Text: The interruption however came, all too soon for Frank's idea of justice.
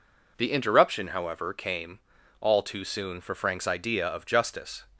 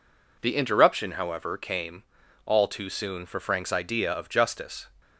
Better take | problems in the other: neither | none

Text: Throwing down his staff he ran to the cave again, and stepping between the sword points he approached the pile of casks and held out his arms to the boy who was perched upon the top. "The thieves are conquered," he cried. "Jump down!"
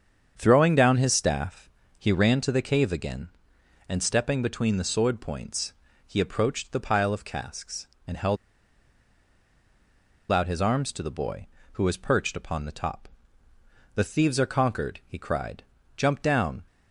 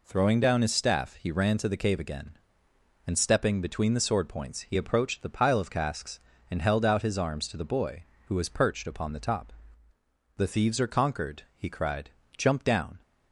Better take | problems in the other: second | starts louder than the rest; strong; until 1.3 s; 7.5 dB // pauses between "staff" and "he"; slight; at 1.6 s; 0.28 s long // pauses between "points" and "he"; slight; at 5.7 s; 0.32 s long // pauses between "held" and "out"; strong; at 8.3 s; 1.9 s long

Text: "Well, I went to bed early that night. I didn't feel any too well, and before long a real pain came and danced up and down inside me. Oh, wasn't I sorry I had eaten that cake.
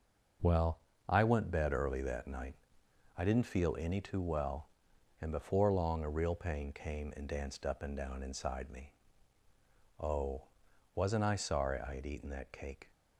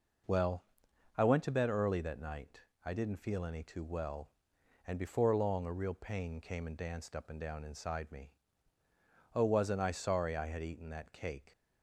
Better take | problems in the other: second | skips "to"; at 1.5 s

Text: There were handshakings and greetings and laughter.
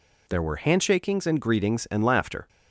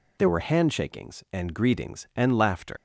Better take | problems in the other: first | leaves "laughter" unfinished; at 2.7 s; 110 ms

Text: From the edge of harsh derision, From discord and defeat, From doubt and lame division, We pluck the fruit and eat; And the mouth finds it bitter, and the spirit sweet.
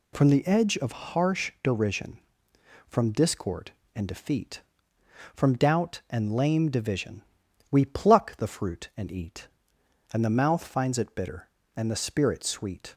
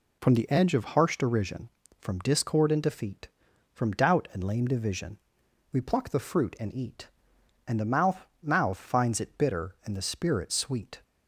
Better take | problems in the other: first | says "mouth" twice; at 8.4 s

